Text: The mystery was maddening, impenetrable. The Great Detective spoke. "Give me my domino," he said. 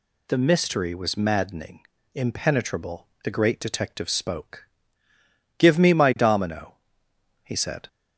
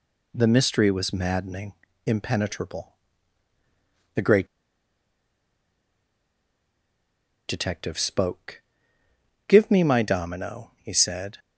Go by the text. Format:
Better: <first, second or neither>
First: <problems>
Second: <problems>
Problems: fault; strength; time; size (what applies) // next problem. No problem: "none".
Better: first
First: none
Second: pauses between "Great" and "Detective"; strong; at 4.4 s; 3.0 s long